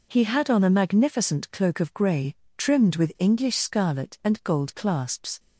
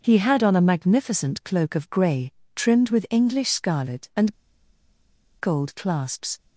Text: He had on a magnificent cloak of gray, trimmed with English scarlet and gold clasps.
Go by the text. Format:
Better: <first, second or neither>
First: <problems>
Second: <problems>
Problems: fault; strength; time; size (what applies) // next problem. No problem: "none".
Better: first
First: none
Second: pauses between "and" and "gold"; at 4.3 s; 1.0 s long